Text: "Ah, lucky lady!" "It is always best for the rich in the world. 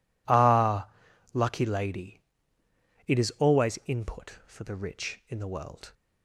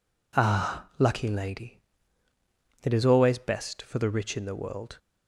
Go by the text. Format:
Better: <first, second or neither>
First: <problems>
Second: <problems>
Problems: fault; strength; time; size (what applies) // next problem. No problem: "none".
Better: second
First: says "input" for "best"; at 3.8 s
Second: none